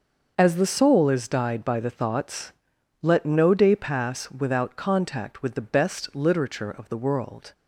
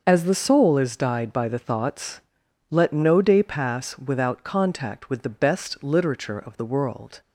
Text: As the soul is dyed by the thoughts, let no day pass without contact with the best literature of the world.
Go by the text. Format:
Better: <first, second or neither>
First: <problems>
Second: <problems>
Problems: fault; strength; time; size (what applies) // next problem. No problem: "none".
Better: neither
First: starts louder than the rest; until 1.3 s; 6 dB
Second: starts louder than the rest; until 1.0 s; 6 dB